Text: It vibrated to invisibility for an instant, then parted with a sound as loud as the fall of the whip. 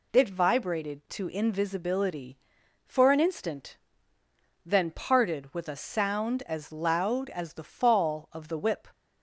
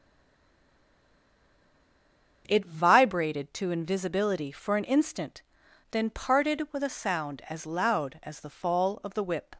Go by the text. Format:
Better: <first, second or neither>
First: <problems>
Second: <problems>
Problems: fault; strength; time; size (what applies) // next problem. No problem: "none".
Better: first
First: none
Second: stays silent before the first word; until 2.4 s; 2.4 s long // starts louder than the rest; until 3.4 s; 7 dB